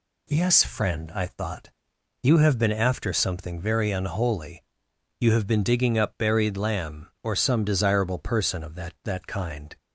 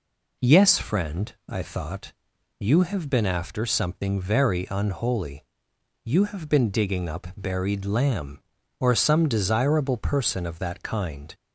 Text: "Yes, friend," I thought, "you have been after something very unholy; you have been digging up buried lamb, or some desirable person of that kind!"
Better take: second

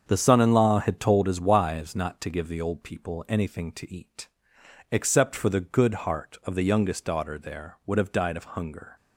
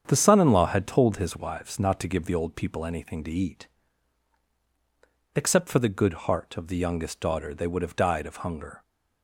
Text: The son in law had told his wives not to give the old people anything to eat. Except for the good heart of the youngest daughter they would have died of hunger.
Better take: second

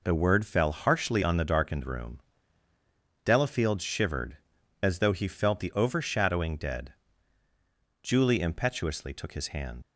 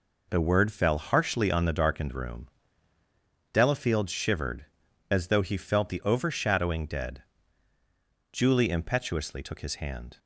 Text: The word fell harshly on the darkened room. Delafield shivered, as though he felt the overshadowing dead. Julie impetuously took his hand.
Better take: second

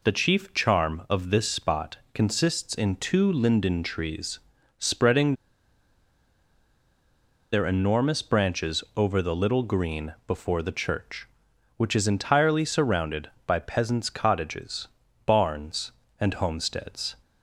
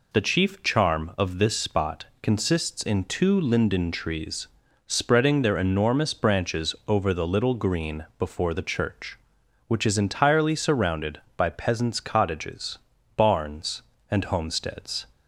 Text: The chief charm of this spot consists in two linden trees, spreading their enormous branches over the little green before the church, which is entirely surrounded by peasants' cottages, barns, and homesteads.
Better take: second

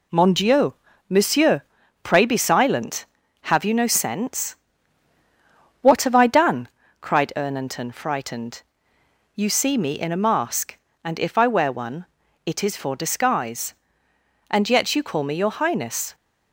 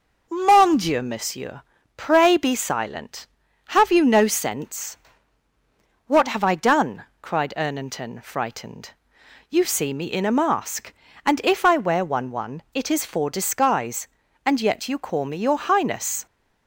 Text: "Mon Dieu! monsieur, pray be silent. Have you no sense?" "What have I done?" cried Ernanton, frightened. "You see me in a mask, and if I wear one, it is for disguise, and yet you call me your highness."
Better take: first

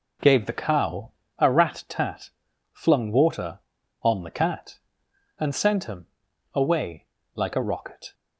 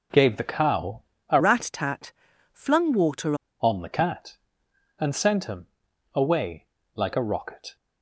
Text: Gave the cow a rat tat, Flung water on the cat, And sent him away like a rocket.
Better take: first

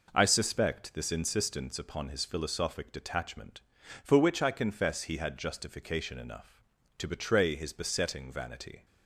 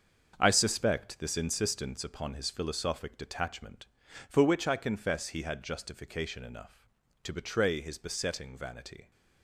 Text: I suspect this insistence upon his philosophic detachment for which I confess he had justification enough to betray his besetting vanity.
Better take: first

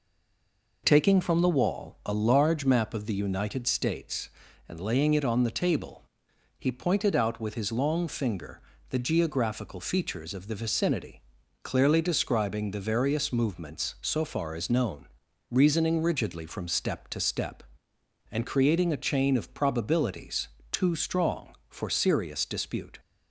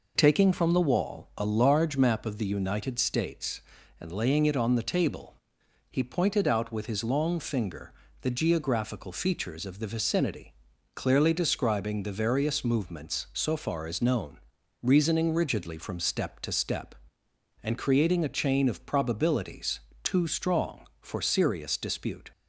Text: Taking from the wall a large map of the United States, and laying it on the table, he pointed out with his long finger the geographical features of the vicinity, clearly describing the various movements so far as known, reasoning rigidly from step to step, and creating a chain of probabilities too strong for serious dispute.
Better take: second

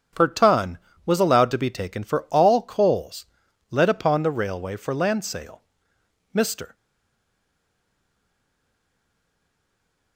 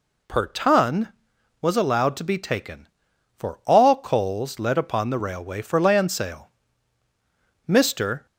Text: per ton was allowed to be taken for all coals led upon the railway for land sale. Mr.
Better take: second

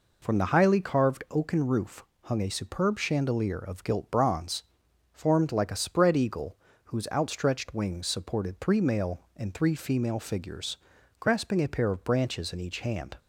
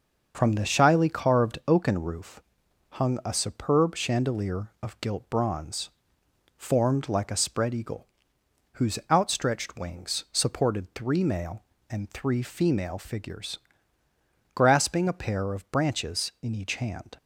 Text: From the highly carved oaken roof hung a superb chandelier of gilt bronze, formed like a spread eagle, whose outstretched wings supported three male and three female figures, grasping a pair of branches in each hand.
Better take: first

